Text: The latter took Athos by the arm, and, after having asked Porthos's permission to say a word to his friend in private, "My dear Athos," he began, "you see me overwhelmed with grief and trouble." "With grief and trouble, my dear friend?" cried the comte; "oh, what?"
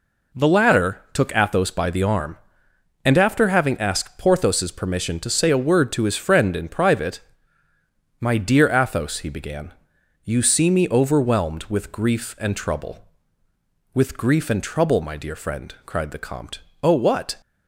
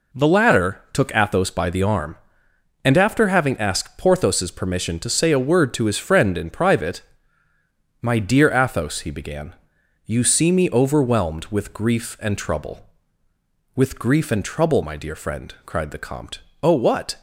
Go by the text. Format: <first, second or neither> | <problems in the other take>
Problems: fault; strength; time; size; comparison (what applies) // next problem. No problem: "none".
neither | none